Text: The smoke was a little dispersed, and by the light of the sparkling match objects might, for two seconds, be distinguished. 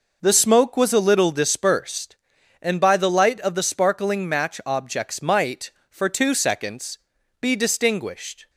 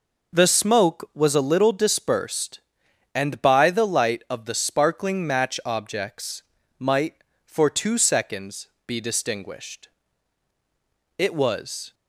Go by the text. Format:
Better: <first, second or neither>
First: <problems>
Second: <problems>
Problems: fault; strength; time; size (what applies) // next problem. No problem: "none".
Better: first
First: none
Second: pauses between "objects" and "might"; at 6.4 s; 0.38 s long // goes on to say "It was"; noticeable; from 11.1 s on; 0.74 s long